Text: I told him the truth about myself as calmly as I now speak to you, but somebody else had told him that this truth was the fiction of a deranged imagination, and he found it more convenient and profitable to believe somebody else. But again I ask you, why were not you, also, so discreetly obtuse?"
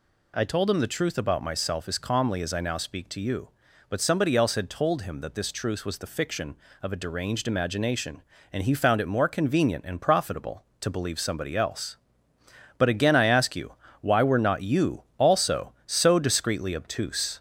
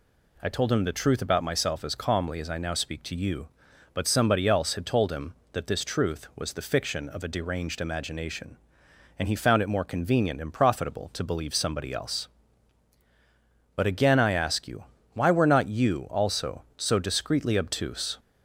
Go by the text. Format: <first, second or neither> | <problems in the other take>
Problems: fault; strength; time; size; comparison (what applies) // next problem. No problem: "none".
second | gets louder; slight; throughout; 3 dB